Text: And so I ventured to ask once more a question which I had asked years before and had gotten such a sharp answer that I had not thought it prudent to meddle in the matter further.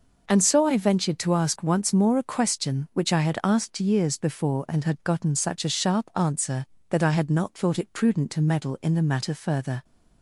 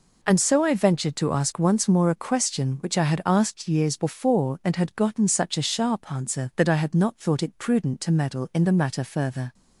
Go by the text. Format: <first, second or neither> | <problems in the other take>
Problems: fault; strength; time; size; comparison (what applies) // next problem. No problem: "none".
neither | none